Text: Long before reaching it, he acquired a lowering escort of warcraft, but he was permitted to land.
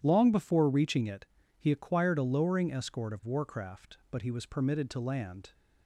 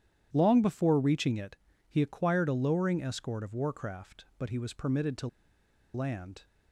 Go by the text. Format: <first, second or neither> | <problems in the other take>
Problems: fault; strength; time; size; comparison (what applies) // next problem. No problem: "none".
first | pauses between "to" and "land"; noticeable; at 5.2 s; 0.67 s long